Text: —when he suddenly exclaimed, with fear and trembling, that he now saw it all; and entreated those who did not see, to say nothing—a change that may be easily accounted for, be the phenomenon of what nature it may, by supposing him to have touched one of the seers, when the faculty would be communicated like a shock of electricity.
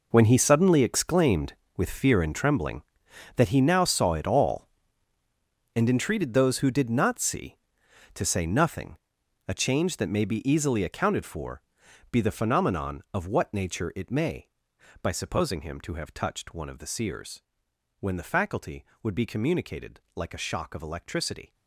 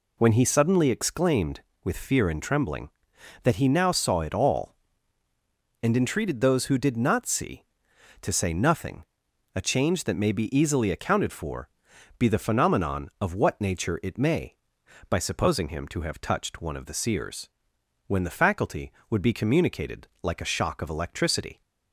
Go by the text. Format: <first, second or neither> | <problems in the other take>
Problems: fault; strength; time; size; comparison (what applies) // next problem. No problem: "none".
second | gets quieter; strong; throughout; 14.5 dB